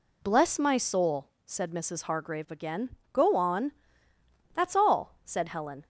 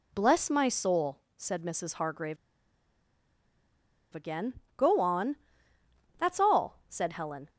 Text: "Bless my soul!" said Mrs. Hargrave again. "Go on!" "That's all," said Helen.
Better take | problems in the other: first | pauses between "Hargrave" and "again"; strong; at 2.3 s; 1.7 s long

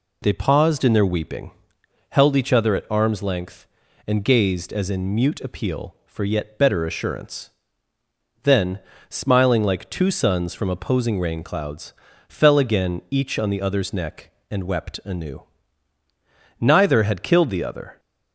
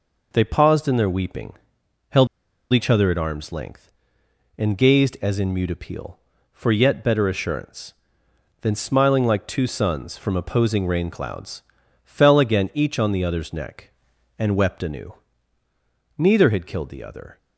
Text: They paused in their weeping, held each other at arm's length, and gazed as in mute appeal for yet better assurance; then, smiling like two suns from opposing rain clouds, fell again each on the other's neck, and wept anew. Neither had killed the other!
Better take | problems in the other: first | pauses between "held" and "each"; noticeable; at 2.2 s; 0.46 s long

